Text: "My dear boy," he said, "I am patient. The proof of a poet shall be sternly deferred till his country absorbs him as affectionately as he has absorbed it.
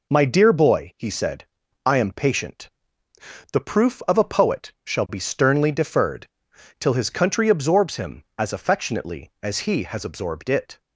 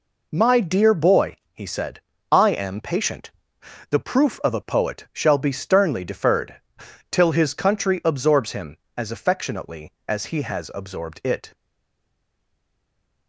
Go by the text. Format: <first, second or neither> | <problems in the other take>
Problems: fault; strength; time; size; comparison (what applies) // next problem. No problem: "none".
first | pauses between "deferred" and "till"; noticeable; at 6.6 s; 0.48 s long; noticeable in the first // stays silent after the last word; noticeable; from 11.5 s on; 1.7 s long